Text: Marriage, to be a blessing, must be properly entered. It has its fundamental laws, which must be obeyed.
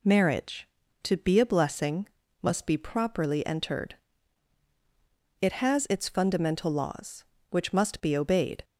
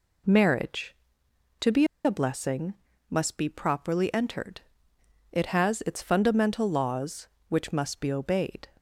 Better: first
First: none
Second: pauses between "be" and "a"; slight; at 1.8 s; 0.20 s long

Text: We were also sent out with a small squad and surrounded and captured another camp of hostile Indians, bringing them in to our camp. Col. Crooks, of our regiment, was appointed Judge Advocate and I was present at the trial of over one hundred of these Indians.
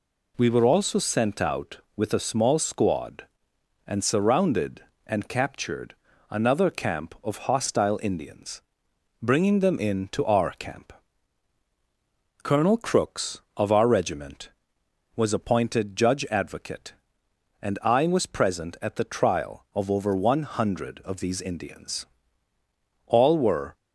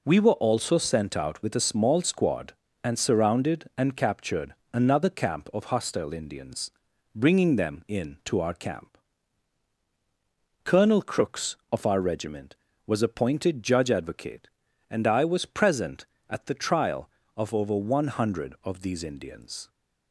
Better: second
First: pauses between "captured" and "another"; slight; at 5.9 s; 0.34 s long // goes on to say "All were"; noticeable; from 23.0 s on; 0.70 s long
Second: pauses between "captured" and "another"; slight; at 4.5 s; 0.18 s long

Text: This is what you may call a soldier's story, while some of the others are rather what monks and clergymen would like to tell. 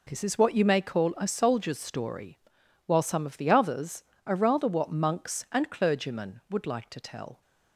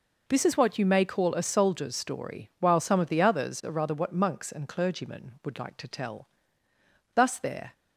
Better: first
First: none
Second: goes on to say "Thus there"; from 7.1 s on; 0.58 s long

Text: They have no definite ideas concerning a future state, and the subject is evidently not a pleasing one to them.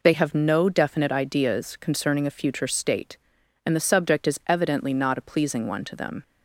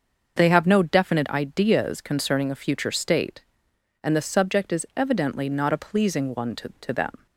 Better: first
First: none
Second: starts louder than the rest; until 1.4 s; 6.5 dB // says "to" twice; at 6.8 s

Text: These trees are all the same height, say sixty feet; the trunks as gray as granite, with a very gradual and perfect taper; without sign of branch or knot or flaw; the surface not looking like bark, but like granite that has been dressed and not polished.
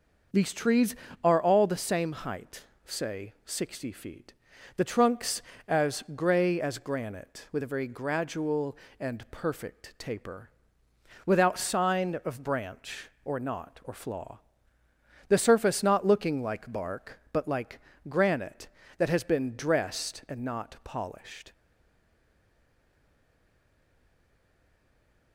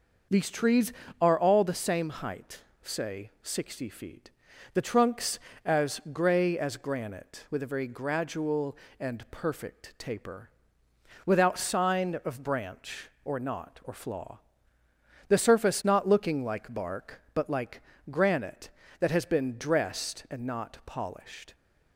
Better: second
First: starts louder than the rest; until 1.6 s; 6 dB // pauses between "like" and "granite"; slight; at 17.7 s; 0.28 s long // stays silent after the last word; strong; from 21.5 s on; 3.8 s long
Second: starts louder than the rest; until 1.5 s; 6 dB // pauses between "like" and "granite"; slight; at 17.8 s; 0.28 s long

